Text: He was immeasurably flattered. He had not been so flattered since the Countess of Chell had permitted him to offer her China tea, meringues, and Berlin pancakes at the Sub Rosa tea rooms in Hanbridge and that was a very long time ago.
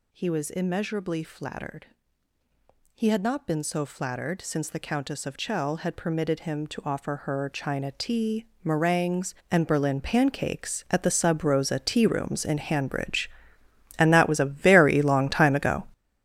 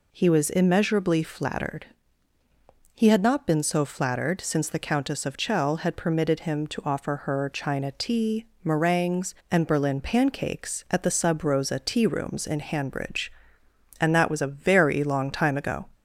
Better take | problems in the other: second | gets louder; strong; throughout; 10 dB

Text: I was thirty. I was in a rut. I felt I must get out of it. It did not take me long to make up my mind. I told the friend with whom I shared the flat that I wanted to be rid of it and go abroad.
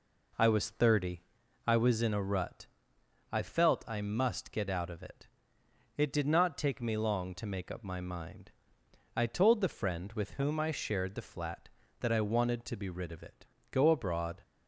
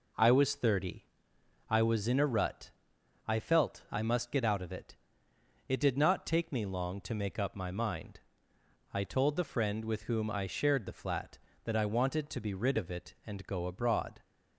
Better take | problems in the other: second | skips "and"; at 13.5 s

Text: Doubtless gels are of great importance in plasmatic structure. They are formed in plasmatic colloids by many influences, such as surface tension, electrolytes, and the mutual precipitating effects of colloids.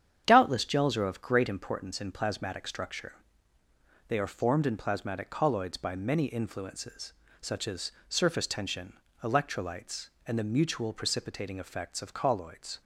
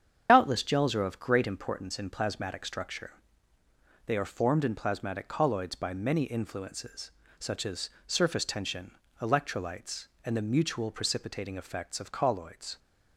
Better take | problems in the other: first | loses the start of "Doubtless"; at 0.2 s; 55 ms // starts louder than the rest; strong; until 1.3 s; 8 dB; strong in the first // pauses between "as" and "surface"; slight; at 7.8 s; 0.18 s long; slight in the first

